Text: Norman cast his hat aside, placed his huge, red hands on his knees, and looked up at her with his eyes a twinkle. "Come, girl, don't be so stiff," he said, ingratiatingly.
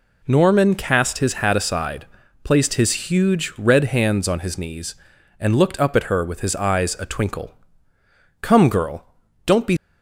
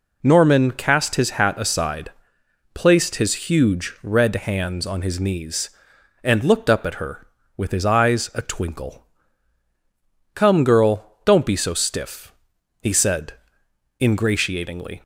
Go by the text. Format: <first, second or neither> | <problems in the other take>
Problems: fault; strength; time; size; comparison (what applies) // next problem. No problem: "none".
second | stops before "so stiff he said ingratiatingly"; at 9.7 s